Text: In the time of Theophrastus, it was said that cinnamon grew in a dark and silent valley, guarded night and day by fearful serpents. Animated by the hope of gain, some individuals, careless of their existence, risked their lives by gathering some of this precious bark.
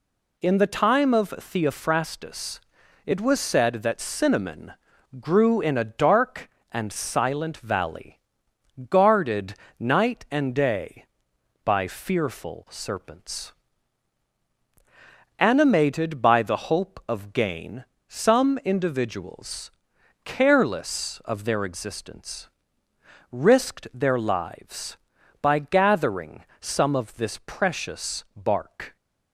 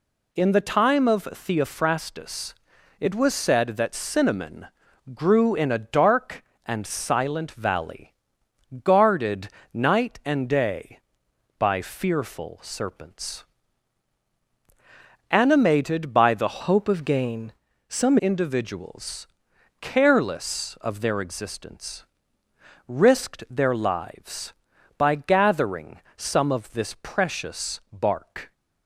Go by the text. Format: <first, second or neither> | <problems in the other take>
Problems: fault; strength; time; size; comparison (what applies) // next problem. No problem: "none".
first | pauses between "cinnamon" and "grew"; noticeable; at 4.6 s; 0.46 s long; noticeable in the first // pauses between "guarded" and "night"; slight; at 9.4 s; 0.24 s long; slight in the first // changes voice from "hope" to "some"; from 16.6 to 18.1 s; 1.5 s long // pauses between "gathering" and "some"; slight; at 25.9 s; 0.18 s long; slight in the first